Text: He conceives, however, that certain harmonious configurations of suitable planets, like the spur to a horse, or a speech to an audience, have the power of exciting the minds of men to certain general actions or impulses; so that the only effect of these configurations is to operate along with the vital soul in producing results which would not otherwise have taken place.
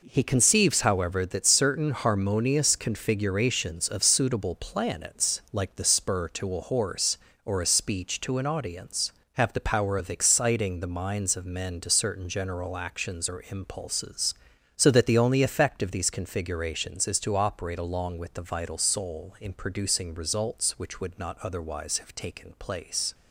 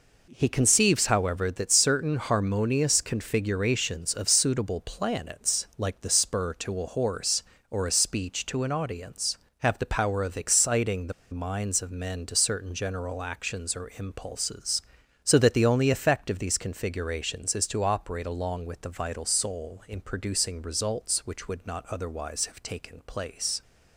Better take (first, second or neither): first